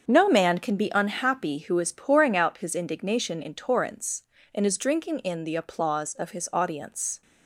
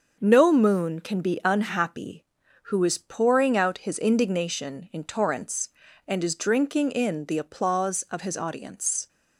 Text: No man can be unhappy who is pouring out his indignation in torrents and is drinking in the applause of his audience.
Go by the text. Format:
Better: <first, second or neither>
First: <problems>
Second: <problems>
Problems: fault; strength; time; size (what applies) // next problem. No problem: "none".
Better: first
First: starts louder than the rest; until 1.1 s; 7 dB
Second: starts louder than the rest; until 1.2 s; 6 dB // says "moon" for "man"; at 0.5 s